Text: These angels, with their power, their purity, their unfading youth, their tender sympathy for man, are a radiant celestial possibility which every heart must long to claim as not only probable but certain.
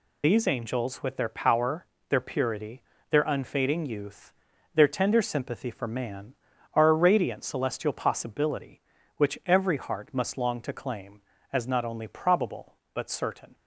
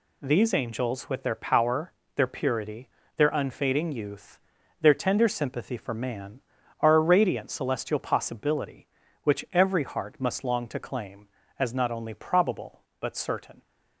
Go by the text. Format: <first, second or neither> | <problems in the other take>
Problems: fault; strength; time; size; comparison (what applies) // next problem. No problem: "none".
second | loses the start of "These"; at 0.2 s; 80 ms